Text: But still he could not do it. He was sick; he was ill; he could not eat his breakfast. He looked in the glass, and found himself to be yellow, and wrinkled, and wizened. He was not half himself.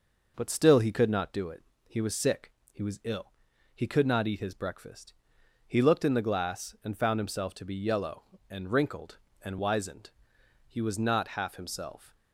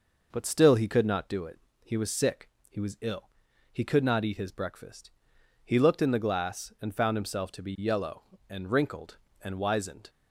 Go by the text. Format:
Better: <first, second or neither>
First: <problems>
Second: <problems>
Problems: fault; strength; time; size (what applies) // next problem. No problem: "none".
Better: first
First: none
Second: stops before "He was not half himself"; at 10.0 s